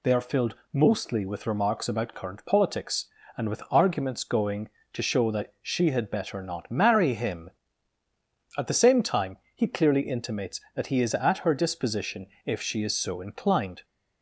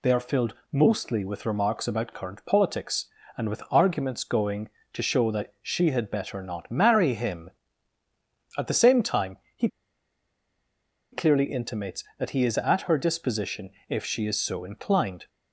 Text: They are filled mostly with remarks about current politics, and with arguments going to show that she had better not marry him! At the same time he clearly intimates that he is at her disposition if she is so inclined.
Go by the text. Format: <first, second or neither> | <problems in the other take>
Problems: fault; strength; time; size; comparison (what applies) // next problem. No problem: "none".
first | pauses between "filled" and "mostly"; slight; at 0.5 s; 0.18 s long; slight in the first // pauses between "time" and "he"; slight; at 9.3 s; 0.18 s long; slight in the first // pauses between "he" and "clearly"; strong; at 9.6 s; 1.4 s long // pauses between "disposition" and "if"; slight; at 13.6 s; 0.18 s long; slight in the first